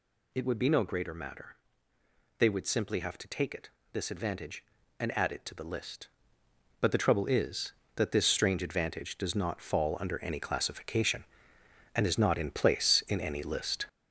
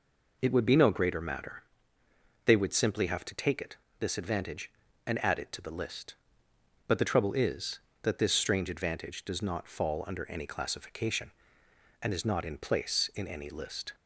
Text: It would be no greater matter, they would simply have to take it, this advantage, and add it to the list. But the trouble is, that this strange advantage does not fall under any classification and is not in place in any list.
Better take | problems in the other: second | gets louder; throughout; 6.5 dB

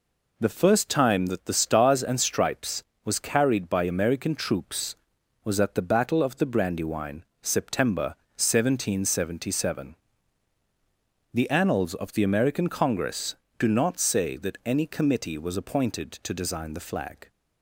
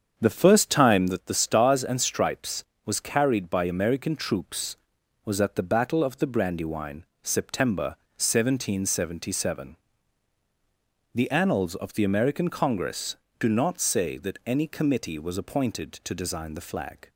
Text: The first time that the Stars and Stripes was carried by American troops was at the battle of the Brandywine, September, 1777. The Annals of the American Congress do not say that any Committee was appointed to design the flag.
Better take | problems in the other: first | starts louder than the rest; strong; until 1.3 s; 7.5 dB

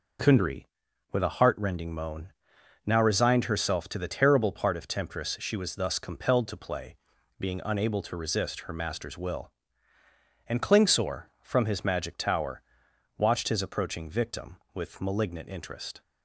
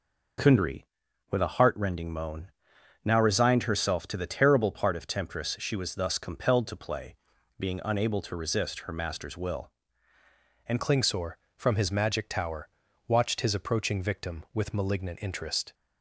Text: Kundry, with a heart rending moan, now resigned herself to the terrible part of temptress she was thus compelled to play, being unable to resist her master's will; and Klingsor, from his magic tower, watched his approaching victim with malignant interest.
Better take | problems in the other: first | changes voice at "Klingsor"; from 10.8 s on; 4.9 s long

